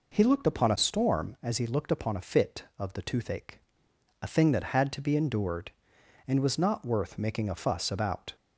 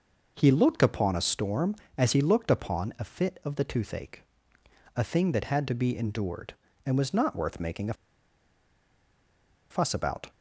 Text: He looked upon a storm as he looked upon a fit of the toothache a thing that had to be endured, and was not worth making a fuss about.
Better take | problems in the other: first | pauses between "toothache" and "a"; noticeable; at 4.2 s; 0.72 s long; noticeable in the first // pauses between "a" and "fuss"; strong; at 7.9 s; 1.7 s long

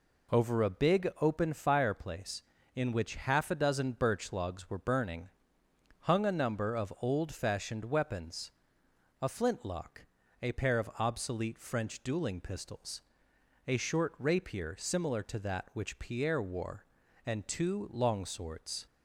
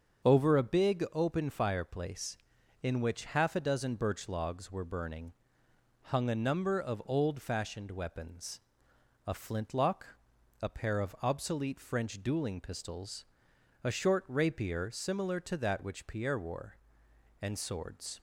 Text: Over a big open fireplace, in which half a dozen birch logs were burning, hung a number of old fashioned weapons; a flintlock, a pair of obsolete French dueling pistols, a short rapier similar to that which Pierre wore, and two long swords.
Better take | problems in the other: first | starts louder than the rest; until 1.3 s; 7 dB // skips "two long"; at 17.5 s

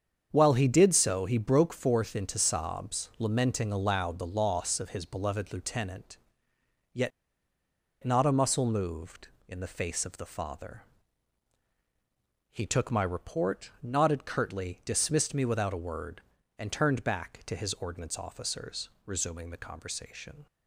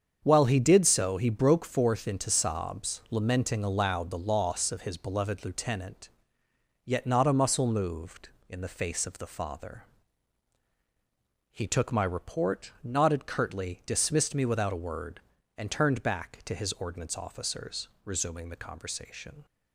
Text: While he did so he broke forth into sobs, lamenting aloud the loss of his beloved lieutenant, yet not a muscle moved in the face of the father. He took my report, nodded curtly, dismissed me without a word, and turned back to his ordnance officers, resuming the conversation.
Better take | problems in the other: second | starts louder than the rest; strong; until 1.3 s; 7.5 dB; strong in the second // pauses between "yet" and "not"; noticeable; at 7.1 s; 0.93 s long

